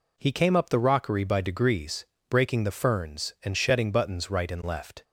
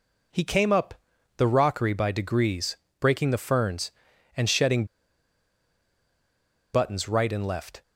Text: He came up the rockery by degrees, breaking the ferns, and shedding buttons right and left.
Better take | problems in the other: first | pauses between "up" and "the"; at 0.9 s; 0.42 s long // pauses between "shedding" and "buttons"; strong; at 4.8 s; 1.8 s long

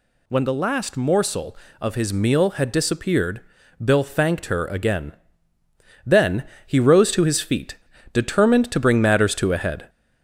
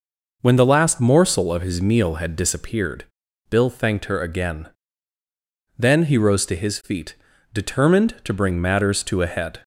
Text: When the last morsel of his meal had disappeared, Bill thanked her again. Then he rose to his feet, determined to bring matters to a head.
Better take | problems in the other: second | gets louder; slight; throughout; 2 dB // pauses between "Then" and "he"; slight; at 6.4 s; 0.22 s long

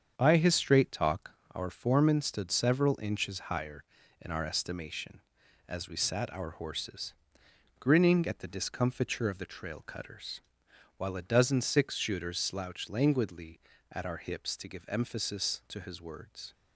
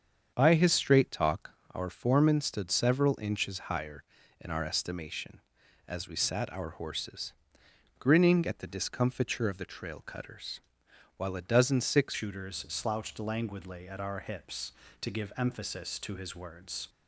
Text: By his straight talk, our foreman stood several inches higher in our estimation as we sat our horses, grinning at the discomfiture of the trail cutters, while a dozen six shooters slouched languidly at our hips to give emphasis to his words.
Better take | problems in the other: first | starts louder than the rest; strong; until 1.3 s; 7.5 dB; strong in the first // changes voice at "shooters"; from 12.1 s on; 4.7 s long

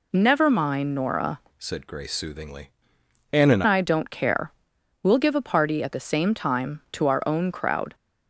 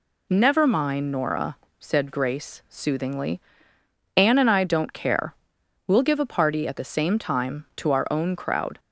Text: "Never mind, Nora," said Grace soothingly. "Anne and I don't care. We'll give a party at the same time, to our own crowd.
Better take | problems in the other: second | changes voice from "said" to "and"; from 1.5 to 3.6 s; 2.1 s long

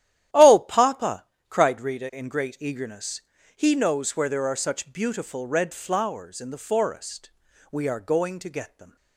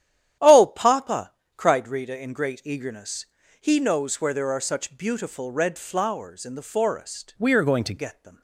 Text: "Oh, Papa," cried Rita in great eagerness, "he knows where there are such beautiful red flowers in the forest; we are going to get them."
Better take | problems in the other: first | starts louder than the rest; strong; until 1.6 s; 10.5 dB; strong in the first // changes voice from "we" to "to"; from 7.3 to 7.9 s; 0.6 s long

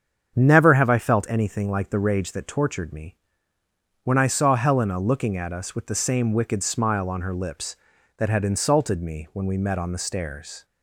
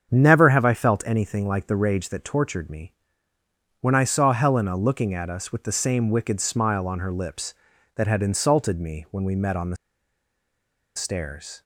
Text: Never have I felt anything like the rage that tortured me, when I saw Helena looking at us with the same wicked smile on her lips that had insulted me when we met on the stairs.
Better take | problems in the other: first | starts louder than the rest; strong; until 1.1 s; 7.5 dB; strong in the first // pauses between "the" and "stairs"; at 9.7 s; 1.1 s long

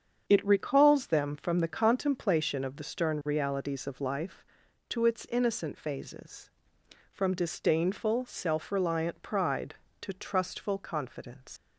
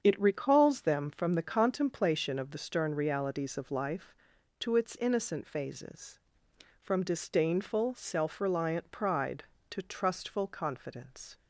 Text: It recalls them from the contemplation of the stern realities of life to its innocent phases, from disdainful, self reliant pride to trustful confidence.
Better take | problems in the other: second | starts louder than the rest; strong; until 1.2 s; 7.5 dB; strong in the second // leaves "confidence" unfinished; at 11.5 s; 120 ms

